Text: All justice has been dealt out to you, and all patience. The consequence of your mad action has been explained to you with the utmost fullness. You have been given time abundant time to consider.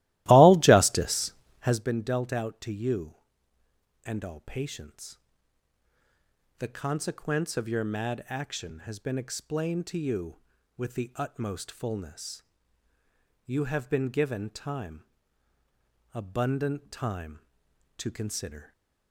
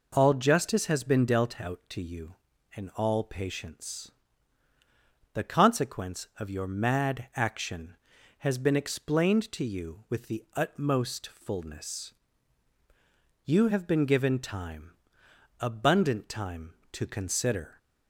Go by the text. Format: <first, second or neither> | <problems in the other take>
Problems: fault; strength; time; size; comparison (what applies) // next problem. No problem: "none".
second | starts louder than the rest; strong; until 1.9 s; 16.5 dB // pauses between "time" and "abundant"; at 15.0 s; 1.0 s long; noticeable in the second